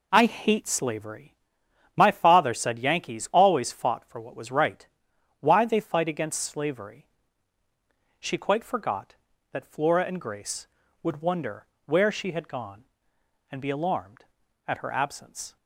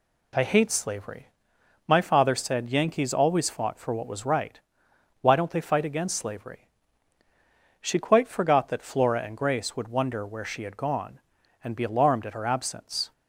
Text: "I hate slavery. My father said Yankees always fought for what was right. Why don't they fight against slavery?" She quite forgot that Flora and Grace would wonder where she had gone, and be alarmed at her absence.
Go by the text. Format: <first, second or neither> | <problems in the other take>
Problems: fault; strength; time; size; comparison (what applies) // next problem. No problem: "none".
second | skips "don't"; at 5.6 s // pauses between "wonder" and "where"; slight; at 11.6 s; 0.20 s long